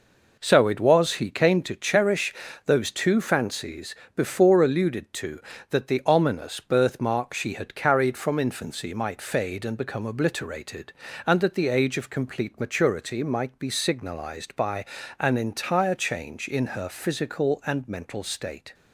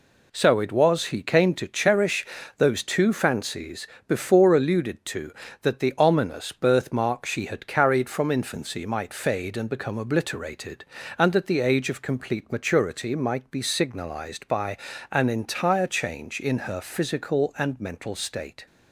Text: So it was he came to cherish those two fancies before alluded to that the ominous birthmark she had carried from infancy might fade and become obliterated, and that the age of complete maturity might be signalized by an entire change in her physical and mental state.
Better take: second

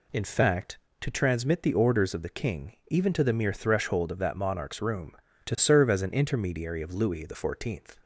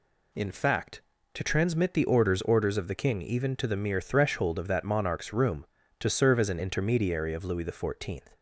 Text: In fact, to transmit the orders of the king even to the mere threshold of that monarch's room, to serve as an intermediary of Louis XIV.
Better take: first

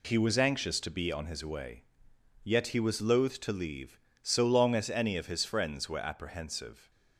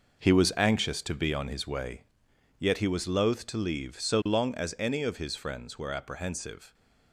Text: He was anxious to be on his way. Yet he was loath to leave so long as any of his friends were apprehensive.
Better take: first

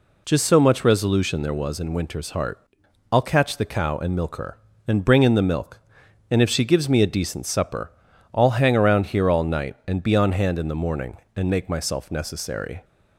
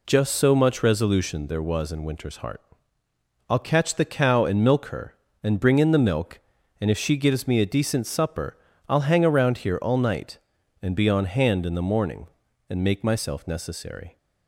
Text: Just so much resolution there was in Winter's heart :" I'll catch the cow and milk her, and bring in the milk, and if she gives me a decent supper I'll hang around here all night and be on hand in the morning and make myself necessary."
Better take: neither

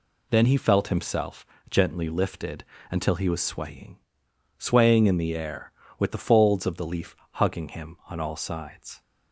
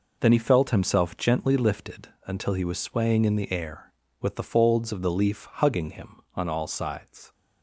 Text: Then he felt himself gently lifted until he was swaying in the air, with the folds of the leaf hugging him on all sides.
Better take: second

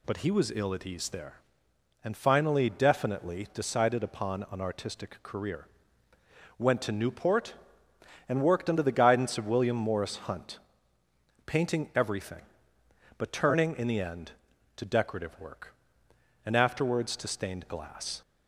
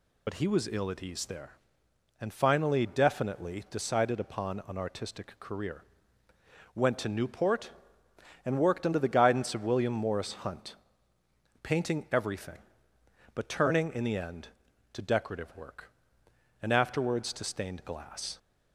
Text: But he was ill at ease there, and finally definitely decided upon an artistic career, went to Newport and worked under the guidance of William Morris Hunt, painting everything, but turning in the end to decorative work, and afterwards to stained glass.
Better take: first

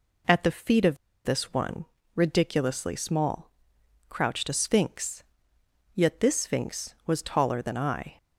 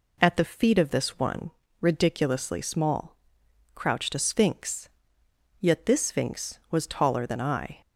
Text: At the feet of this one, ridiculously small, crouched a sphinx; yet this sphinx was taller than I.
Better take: second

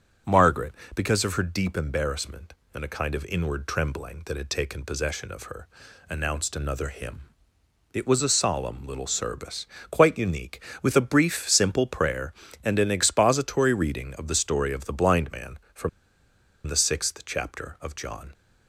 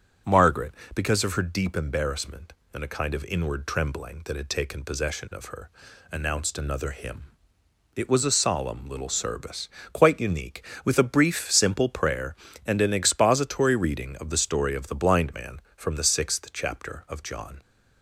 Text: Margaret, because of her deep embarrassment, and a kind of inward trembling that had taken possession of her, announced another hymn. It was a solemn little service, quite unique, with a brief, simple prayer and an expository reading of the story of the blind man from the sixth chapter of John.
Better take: second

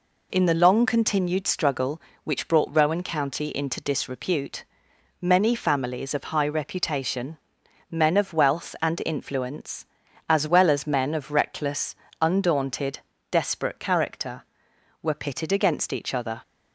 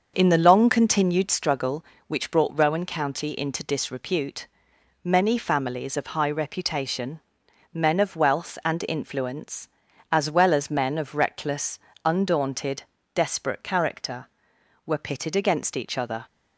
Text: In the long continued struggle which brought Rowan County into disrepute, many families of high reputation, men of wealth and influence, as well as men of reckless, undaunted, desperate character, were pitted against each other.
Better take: first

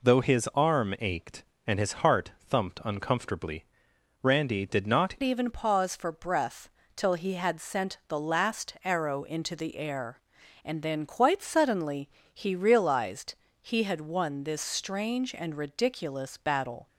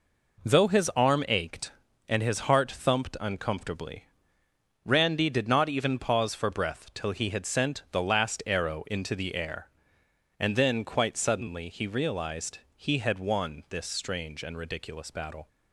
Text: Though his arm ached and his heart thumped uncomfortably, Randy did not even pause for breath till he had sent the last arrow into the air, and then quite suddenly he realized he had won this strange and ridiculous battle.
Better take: second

